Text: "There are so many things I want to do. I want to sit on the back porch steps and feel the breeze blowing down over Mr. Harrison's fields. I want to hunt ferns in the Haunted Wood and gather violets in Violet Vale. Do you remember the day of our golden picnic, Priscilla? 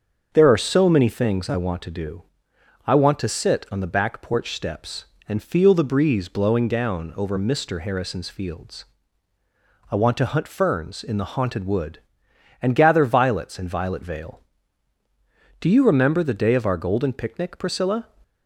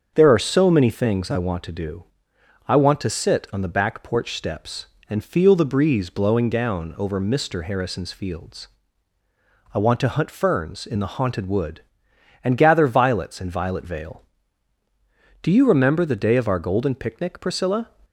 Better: neither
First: starts louder than the rest; until 1.3 s; 7 dB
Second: starts louder than the rest; until 1.1 s; 7 dB

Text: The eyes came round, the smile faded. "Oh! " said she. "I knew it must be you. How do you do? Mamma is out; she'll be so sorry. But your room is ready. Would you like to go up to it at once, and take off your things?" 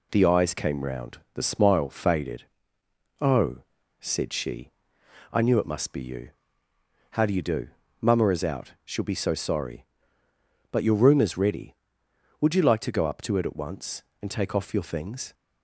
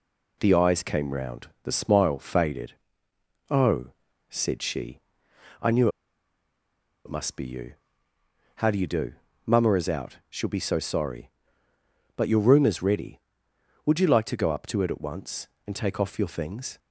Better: first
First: none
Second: pauses between "knew" and "it"; at 5.8 s; 1.1 s long

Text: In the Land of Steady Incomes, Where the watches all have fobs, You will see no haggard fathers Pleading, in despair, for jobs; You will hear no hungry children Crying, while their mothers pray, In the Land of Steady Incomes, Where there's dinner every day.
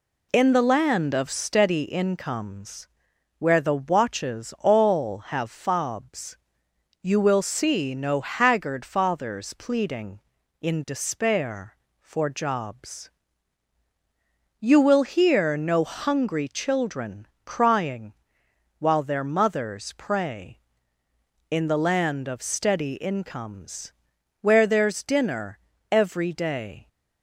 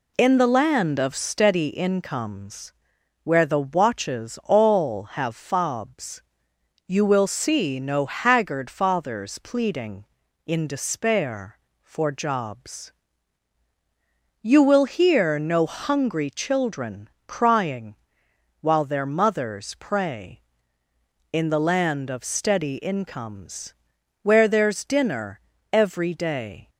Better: neither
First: pauses between "children" and "Crying"; slight; at 17.2 s; 0.18 s long // pauses between "dinner" and "every"; slight; at 25.5 s; 0.32 s long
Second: pauses between "children" and "Crying"; slight; at 17.0 s; 0.18 s long // pauses between "dinner" and "every"; slight; at 25.3 s; 0.32 s long

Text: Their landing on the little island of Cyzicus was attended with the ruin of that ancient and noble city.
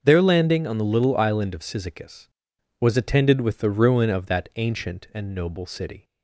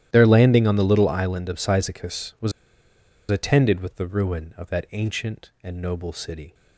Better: first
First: starts louder than the rest; until 1.0 s; 6.5 dB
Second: starts louder than the rest; strong; until 1.1 s; 12.5 dB // pauses between "was" and "attended"; noticeable; at 2.5 s; 0.78 s long

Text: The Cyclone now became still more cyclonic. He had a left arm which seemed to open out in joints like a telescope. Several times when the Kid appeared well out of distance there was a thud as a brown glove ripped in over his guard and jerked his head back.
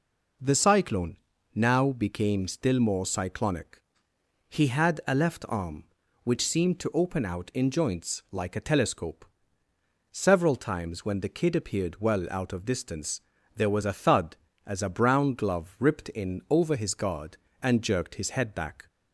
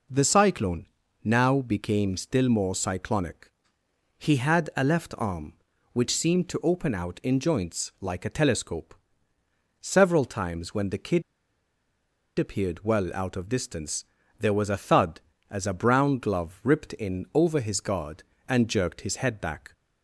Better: first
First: pauses between "Cyclone" and "now"; at 1.1 s; 0.38 s long // pauses between "distance" and "there"; slight; at 13.2 s; 0.34 s long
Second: pauses between "Cyclone" and "now"; at 0.8 s; 0.38 s long // pauses between "Kid" and "appeared"; at 11.2 s; 1.1 s long // pauses between "distance" and "there"; slight; at 14.0 s; 0.34 s long

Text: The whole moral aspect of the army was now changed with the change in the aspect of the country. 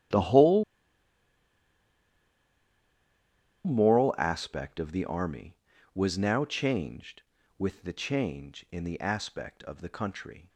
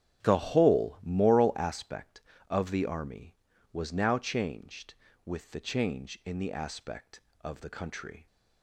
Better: second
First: starts louder than the rest; strong; until 4.1 s; 12.5 dB // pauses between "whole" and "moral"; strong; at 0.6 s; 3.0 s long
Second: starts louder than the rest; strong; until 1.2 s; 9 dB

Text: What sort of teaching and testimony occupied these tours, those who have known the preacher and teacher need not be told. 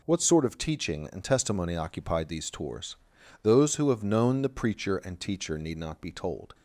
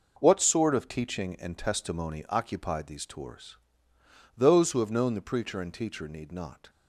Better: first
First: none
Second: stops before "be told"; at 6.6 s

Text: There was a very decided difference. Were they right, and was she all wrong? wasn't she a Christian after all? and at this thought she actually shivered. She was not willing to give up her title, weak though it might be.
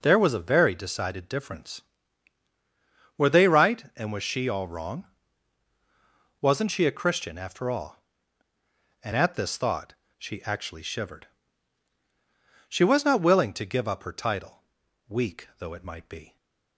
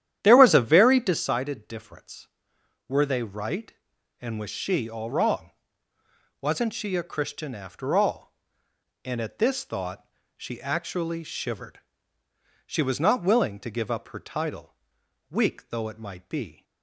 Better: first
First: pauses between "thought" and "she"; slight; at 9.9 s; 0.26 s long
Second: starts louder than the rest; strong; until 1.4 s; 10.5 dB // pauses between "thought" and "she"; slight; at 10.0 s; 0.28 s long

